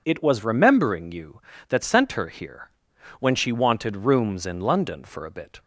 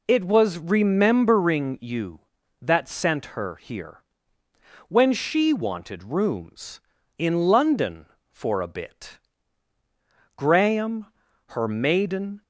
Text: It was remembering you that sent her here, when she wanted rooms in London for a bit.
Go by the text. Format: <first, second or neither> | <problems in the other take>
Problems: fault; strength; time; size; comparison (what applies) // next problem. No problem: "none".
first | goes on to say "Graham her maiden"; strong; from 10.3 s on; 2.0 s long